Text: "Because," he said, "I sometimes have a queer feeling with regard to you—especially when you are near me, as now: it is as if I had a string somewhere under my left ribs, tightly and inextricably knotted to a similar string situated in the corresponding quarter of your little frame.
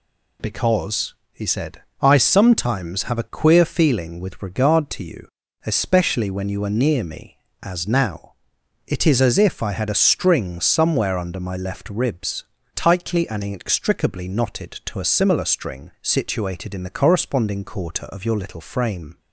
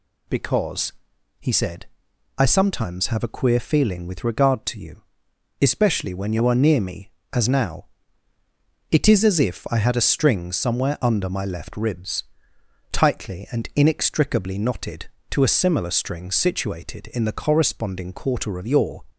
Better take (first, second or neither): first